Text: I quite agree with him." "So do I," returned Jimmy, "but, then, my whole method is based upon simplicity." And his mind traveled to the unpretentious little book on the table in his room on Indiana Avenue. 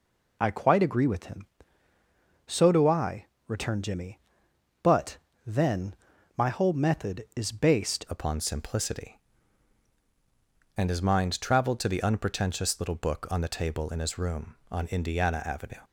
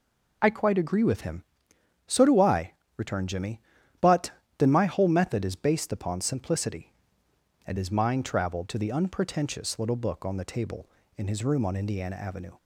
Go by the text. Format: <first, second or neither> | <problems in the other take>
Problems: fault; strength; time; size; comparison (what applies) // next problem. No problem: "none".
second | changes voice at "upon"; from 8.0 s on; 7.8 s long